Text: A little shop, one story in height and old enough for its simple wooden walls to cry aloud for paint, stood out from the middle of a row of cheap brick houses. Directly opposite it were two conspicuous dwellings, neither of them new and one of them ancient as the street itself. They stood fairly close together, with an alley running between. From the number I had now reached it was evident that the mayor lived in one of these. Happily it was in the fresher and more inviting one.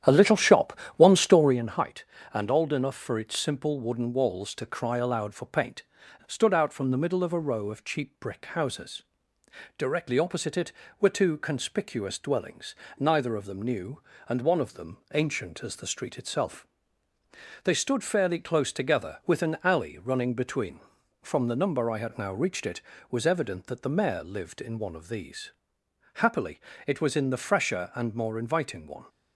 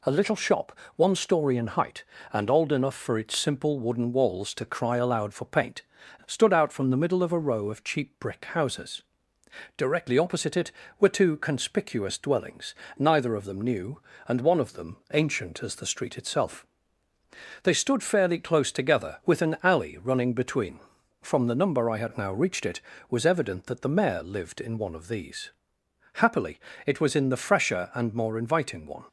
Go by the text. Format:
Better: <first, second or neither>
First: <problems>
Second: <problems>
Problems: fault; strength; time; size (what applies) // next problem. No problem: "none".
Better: second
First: starts louder than the rest; strong; until 1.6 s; 10 dB // pauses between "them" and "ancient"; slight; at 14.9 s; 0.16 s long // pauses between "Happily" and "it"; slight; at 26.5 s; 0.28 s long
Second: pauses between "them" and "ancient"; slight; at 14.9 s; 0.16 s long // pauses between "Happily" and "it"; slight; at 26.5 s; 0.28 s long